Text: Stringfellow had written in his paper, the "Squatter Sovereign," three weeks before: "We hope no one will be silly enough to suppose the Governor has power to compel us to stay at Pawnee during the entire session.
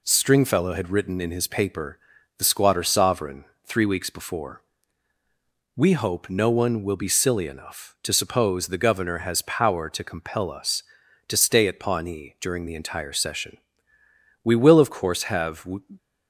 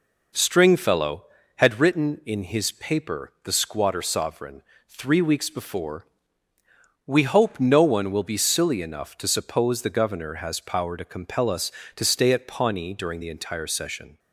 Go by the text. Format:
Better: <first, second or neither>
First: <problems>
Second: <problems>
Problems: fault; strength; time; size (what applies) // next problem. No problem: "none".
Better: second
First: goes on to say "We will of course have"; noticeable; from 14.4 s on; 1.2 s long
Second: none